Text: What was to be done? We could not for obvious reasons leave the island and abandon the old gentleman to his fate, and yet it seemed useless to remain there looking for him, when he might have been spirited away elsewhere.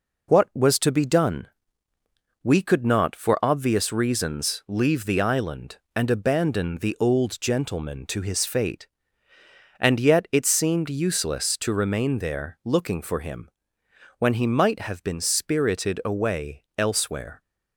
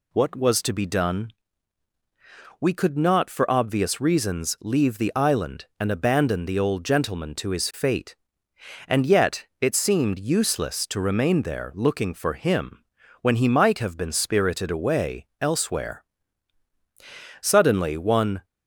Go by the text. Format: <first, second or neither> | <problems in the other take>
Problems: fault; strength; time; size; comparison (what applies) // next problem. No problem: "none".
first | goes on to say "Suddenly one"; noticeable; from 17.4 s on; 1.0 s long